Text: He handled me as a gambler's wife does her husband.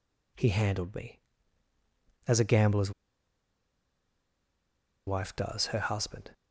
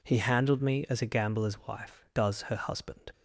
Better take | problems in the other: second | pauses between "gambler's" and "wife"; strong; at 2.9 s; 2.1 s long

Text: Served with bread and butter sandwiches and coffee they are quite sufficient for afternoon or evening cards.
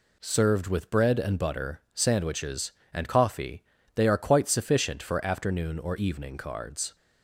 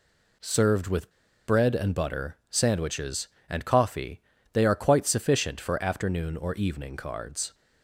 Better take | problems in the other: first | pauses between "with" and "bread"; at 1.1 s; 0.37 s long // pauses between "coffee" and "they"; slight; at 4.2 s; 0.34 s long; slight in the first

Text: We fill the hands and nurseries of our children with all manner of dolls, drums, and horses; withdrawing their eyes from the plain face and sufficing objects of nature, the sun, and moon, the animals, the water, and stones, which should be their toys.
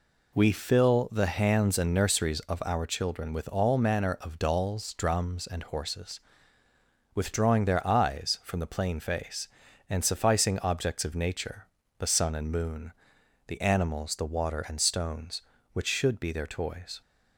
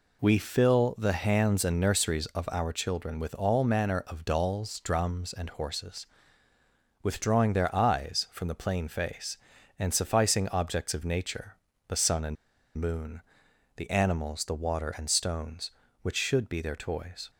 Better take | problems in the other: first | pauses between "and" and "moon"; at 12.3 s; 0.42 s long

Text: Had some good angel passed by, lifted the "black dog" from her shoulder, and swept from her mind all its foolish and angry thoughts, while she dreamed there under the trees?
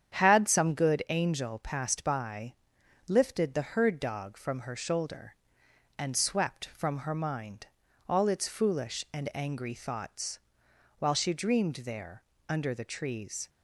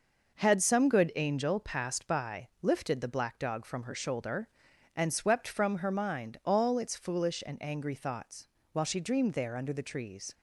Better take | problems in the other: second | starts louder than the rest; strong; until 1.2 s; 9 dB // says "herd" for "black"; at 3.6 s // pauses between "mind" and "all"; at 7.6 s; 0.42 s long // pauses between "there" and "under"; slight; at 12.2 s; 0.26 s long

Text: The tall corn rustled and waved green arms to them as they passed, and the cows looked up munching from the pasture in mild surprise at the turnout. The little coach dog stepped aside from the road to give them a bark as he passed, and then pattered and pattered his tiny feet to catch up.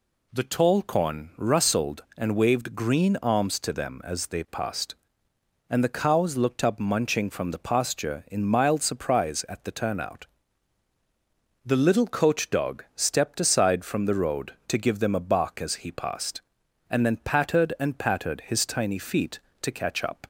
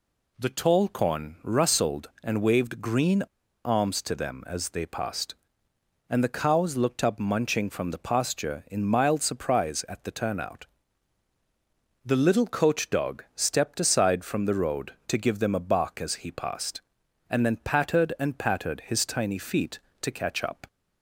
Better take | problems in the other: first | pauses between "green" and "arms"; at 3.2 s; 0.42 s long

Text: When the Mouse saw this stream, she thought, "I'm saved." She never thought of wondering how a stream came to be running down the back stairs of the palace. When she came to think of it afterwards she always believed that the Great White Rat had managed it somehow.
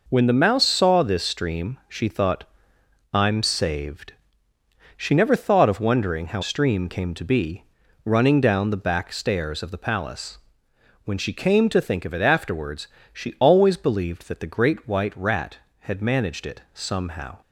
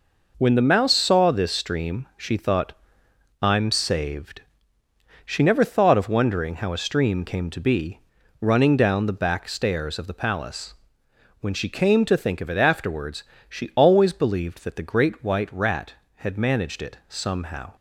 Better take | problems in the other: second | skips "a"; at 6.4 s // pauses between "be" and "running"; at 7.6 s; 0.40 s long; also in the second // pauses between "afterwards" and "she"; slight; at 12.8 s; 0.24 s long; slight in the second

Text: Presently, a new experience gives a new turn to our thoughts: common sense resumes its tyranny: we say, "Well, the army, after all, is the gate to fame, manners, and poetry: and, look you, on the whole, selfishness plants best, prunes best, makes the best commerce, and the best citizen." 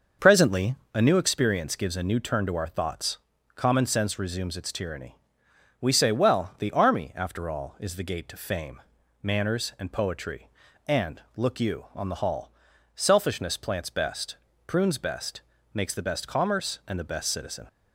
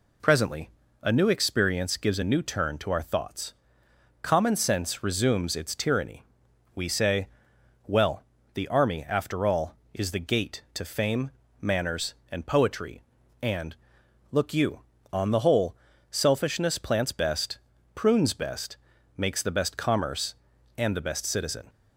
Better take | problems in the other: second | starts louder than the rest; noticeable; until 1.3 s; 6 dB // says "hall" for "whole"; at 12.2 s

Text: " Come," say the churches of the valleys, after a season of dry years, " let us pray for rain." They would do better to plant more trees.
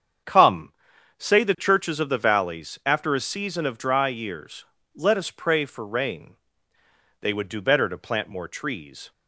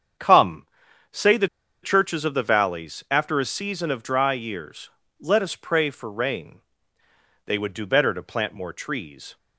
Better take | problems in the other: first | starts louder than the rest; strong; until 2.0 s; 8 dB; strong in the first // pauses between "the" and "churches"; at 1.4 s; 0.36 s long

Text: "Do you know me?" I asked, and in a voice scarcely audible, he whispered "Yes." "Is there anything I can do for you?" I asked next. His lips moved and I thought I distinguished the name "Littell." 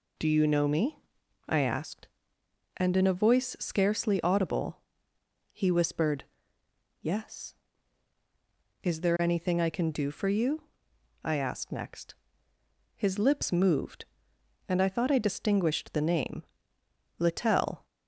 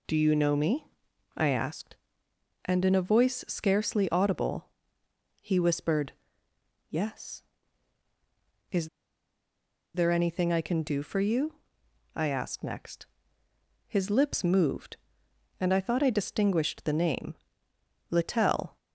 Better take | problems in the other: first | pauses between "whispered" and "Yes"; noticeable; at 6.1 s; 0.78 s long; noticeable in the first // pauses between "Is" and "there"; at 8.8 s; 1.0 s long // pauses between "name" and "Littell"; noticeable; at 17.3 s; 0.76 s long; noticeable in the first

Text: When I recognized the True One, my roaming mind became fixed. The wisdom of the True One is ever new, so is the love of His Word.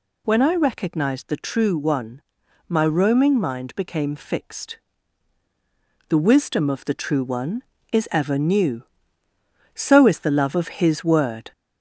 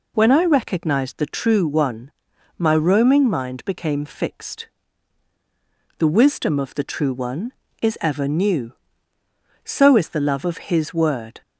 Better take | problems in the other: second | gets louder; slight; throughout; 3 dB

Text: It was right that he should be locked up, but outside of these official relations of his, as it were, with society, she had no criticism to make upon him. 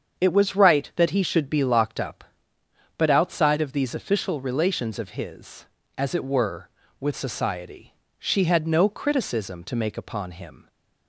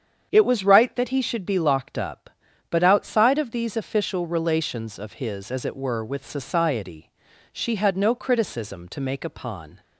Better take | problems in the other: first | starts louder than the rest; strong; until 1.3 s; 8 dB; strong in the first // stops before "him"; at 9.8 s

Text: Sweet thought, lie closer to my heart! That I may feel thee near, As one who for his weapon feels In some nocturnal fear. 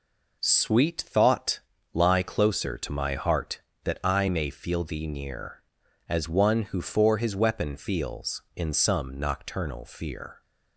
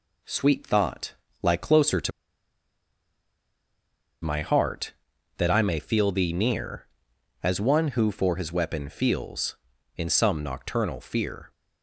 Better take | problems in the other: first | pauses between "to" and "my"; strong; at 2.1 s; 2.1 s long

